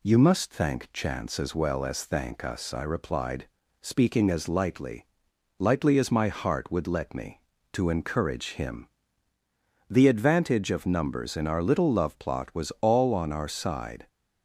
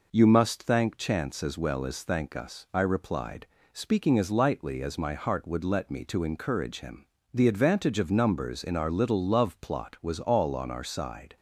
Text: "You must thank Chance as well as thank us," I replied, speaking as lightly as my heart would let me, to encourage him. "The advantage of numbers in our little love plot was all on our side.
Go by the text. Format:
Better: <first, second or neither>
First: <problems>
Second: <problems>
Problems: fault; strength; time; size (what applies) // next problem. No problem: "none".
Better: second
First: says "lightly" twice; at 5.5 s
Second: none